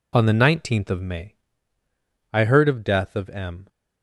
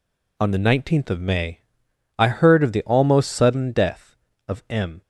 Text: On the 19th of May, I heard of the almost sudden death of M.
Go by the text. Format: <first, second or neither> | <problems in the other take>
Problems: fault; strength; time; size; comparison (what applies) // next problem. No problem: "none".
second | skips "the almost sudden"; at 2.8 s